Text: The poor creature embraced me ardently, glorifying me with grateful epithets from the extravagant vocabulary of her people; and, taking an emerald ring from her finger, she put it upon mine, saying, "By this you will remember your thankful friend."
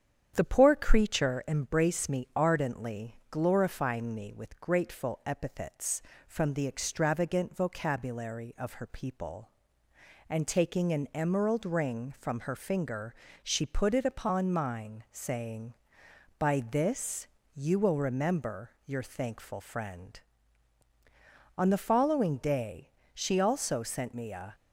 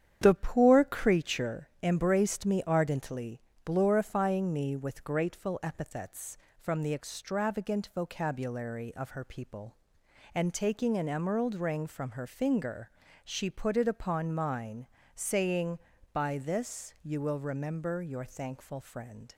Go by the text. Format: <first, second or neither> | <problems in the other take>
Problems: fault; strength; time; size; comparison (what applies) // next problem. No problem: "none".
second | starts louder than the rest; strong; until 1.3 s; 8.5 dB; strong in the second // pauses between "this" and "you"; slight; at 17.2 s; 0.26 s long // pauses between "remember" and "your"; slight; at 18.7 s; 0.16 s long // goes on to say "On the following day she also sent me a"; strong; from 21.5 s on; 2.9 s long